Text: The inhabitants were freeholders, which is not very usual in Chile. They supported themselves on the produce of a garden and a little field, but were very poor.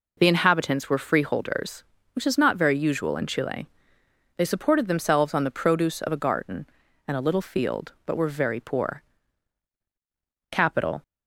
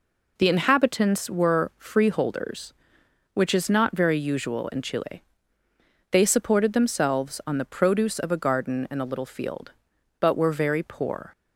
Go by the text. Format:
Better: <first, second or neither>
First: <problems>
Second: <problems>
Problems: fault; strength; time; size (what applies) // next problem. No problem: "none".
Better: second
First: goes on to say "Capital"; from 10.5 s on; 0.52 s long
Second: none